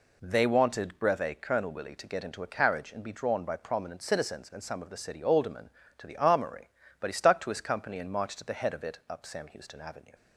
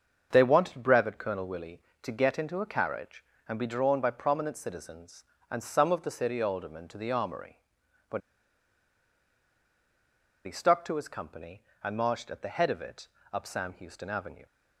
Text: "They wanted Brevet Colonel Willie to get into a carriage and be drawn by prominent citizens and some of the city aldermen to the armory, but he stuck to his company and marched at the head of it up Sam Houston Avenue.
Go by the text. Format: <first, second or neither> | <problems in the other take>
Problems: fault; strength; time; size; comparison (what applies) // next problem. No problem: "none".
first | starts louder than the rest; until 1.3 s; 6.5 dB // pauses between "but" and "he"; strong; at 8.2 s; 2.2 s long // pauses between "it" and "up"; slight; at 13.0 s; 0.26 s long